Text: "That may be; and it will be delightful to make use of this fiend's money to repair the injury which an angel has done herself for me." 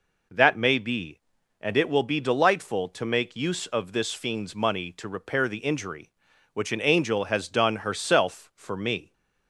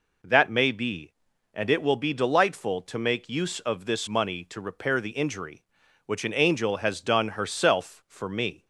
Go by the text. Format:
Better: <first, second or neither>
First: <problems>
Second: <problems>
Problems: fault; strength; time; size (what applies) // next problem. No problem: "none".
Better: first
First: none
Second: skips "fiend's"; at 4.0 s